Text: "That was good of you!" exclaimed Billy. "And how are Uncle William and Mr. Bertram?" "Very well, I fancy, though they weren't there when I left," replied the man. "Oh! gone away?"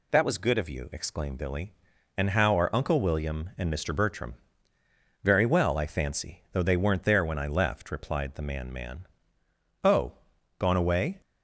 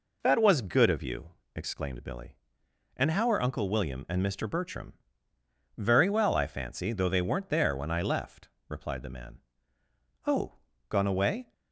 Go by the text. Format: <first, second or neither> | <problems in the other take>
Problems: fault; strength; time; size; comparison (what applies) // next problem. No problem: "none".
second | says "man" twice; at 8.7 s